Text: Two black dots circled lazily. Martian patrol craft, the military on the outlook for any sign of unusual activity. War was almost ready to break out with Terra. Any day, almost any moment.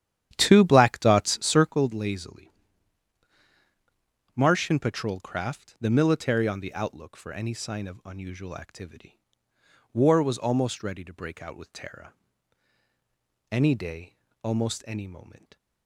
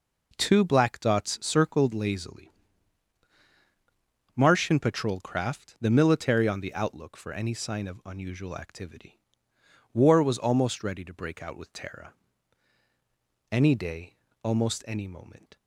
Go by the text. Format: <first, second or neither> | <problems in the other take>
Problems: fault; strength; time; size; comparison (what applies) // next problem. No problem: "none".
second | starts louder than the rest; strong; until 1.7 s; 10.5 dB